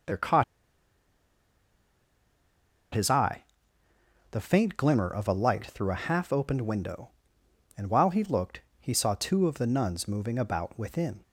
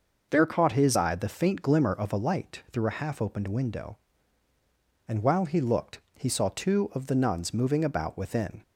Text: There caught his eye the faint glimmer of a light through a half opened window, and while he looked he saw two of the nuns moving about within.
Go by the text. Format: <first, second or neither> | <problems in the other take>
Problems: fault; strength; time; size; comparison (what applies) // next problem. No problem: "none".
second | pauses between "caught" and "his"; strong; at 0.4 s; 2.5 s long // pauses between "eye" and "the"; noticeable; at 3.4 s; 0.88 s long // pauses between "looked" and "he"; slight; at 8.6 s; 0.20 s long; slight in the second